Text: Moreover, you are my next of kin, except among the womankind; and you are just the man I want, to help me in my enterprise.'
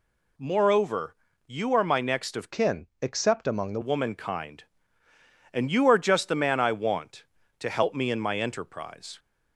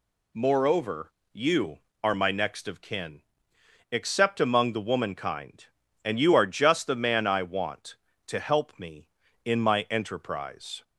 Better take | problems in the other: second | changes voice from "kin" to "the"; from 2.5 to 3.7 s; 1.2 s long

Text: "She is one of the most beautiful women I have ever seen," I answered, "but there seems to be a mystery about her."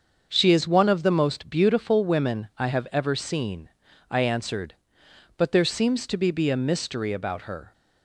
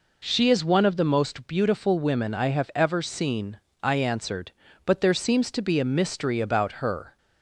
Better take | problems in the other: second | starts louder than the rest; until 1.3 s; 6.5 dB // says "be" twice; at 6.2 s

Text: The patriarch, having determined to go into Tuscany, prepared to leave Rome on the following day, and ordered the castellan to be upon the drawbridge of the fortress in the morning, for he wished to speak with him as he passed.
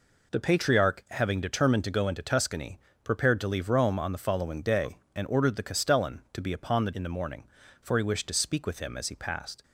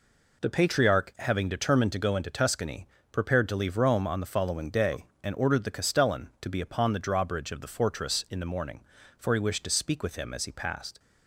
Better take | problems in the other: second | skips "drawbridge of the fortress"; at 6.9 s

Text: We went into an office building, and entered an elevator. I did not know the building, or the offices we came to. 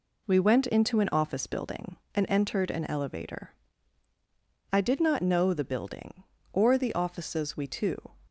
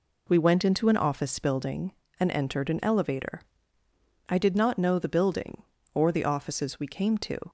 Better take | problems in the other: second | skips "came"; at 7.6 s

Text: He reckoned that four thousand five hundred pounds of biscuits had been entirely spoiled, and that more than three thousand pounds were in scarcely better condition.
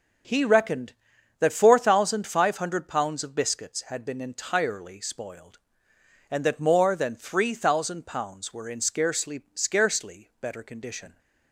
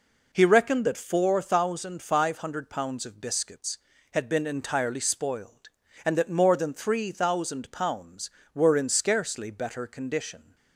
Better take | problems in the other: second | says "scarcely" twice; at 9.5 s

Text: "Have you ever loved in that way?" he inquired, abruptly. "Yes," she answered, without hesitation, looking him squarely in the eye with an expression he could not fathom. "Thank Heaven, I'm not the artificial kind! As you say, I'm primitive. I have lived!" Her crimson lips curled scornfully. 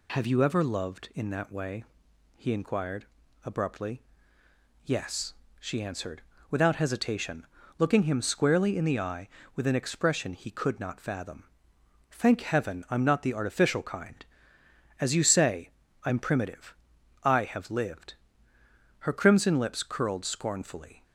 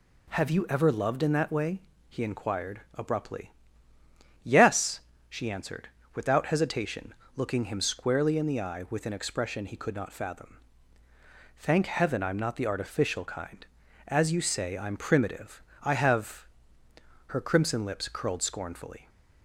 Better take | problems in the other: first | skips "lived"; at 16.8 s

